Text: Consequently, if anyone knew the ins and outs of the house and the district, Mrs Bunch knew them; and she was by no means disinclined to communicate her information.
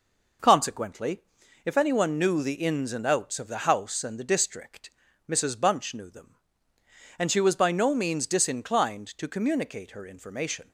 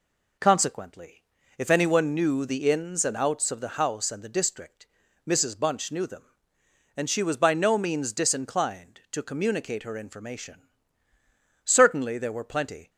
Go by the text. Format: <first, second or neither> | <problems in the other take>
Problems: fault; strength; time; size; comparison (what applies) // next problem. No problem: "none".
first | goes on to say "Certainly there were plenty"; noticeable; from 11.6 s on; 1.2 s long